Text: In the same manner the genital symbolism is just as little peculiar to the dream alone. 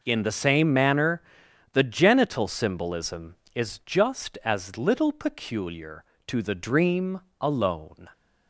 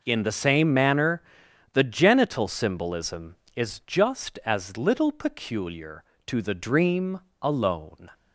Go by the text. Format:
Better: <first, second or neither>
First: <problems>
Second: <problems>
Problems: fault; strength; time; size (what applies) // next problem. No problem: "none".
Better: neither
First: pauses between "manner" and "the"; noticeable; at 1.2 s; 0.52 s long // pauses between "dream" and "alone"; slight; at 7.2 s; 0.20 s long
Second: pauses between "manner" and "the"; noticeable; at 1.2 s; 0.52 s long // pauses between "dream" and "alone"; slight; at 7.2 s; 0.22 s long